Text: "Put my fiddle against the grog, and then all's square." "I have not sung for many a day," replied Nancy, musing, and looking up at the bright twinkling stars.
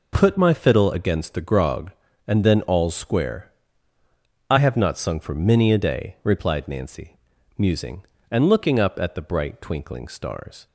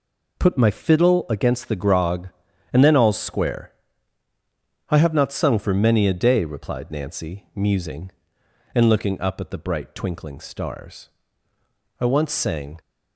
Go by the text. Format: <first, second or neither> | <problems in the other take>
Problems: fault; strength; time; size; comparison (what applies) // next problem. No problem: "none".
first | goes on to say "I once sang"; noticeable; from 11.9 s on; 0.80 s long